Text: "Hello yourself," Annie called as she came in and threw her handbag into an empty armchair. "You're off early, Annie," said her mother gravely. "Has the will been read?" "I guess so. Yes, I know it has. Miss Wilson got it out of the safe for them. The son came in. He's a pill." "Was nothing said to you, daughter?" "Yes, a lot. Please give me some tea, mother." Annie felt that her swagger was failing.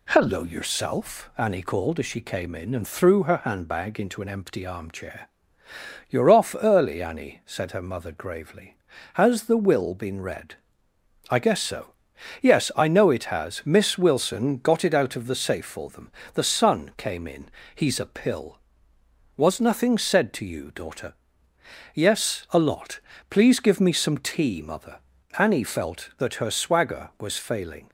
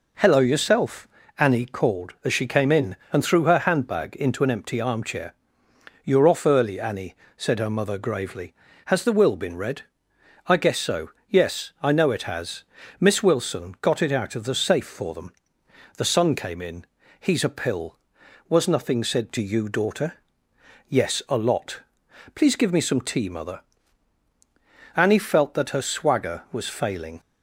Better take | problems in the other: neither | none

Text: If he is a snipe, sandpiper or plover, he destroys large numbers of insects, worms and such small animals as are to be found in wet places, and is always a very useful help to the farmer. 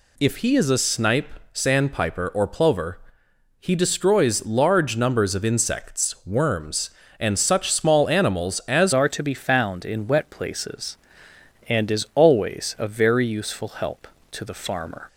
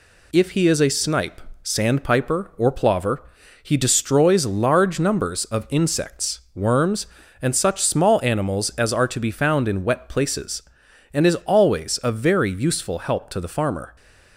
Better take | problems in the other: second | changes voice at "are"; from 8.9 s on; 6.1 s long

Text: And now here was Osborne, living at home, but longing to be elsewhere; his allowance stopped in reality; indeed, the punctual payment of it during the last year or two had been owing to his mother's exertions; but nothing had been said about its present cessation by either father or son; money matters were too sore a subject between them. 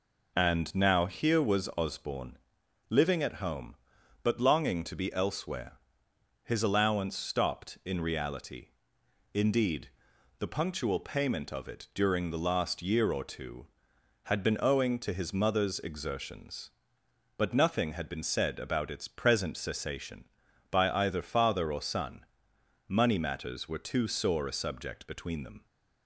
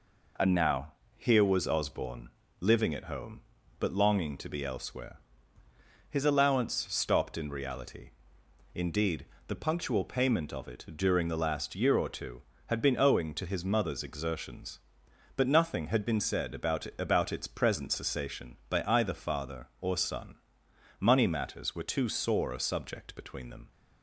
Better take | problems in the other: first | pauses between "now" and "here"; slight; at 0.9 s; 0.24 s long // pauses between "allowance" and "stopped"; slight; at 6.7 s; 0.16 s long // says "about" twice; at 16.9 s

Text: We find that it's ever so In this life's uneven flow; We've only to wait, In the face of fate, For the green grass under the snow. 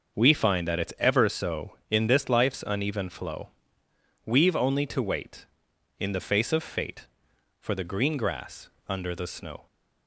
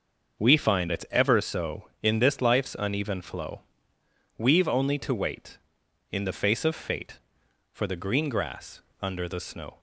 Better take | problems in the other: first | starts louder than the rest; until 1.4 s; 6 dB; also in the first // skips "that"; at 0.9 s // pauses between "grass" and "under"; slight; at 8.8 s; 0.20 s long; slight in the first

